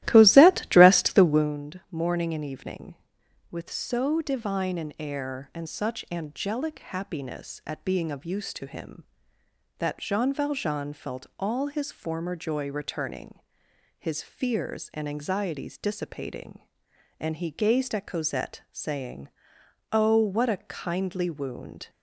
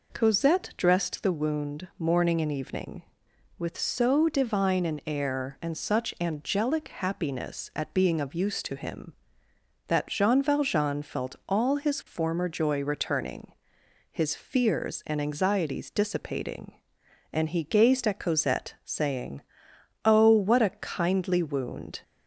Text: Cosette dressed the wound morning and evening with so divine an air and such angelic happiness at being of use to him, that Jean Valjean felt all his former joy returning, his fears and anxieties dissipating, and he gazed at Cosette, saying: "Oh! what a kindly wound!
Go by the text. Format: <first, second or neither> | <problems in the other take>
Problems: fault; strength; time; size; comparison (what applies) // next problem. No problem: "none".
second | starts louder than the rest; strong; until 1.5 s; 15.5 dB